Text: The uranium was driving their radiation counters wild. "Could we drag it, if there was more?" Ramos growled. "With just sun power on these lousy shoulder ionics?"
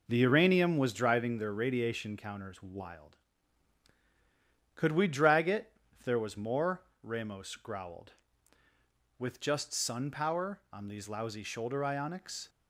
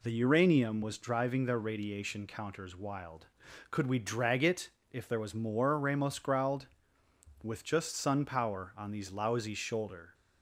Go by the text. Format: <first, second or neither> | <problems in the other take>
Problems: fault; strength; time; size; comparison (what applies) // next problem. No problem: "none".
first | stops before "ionics"; at 10.1 s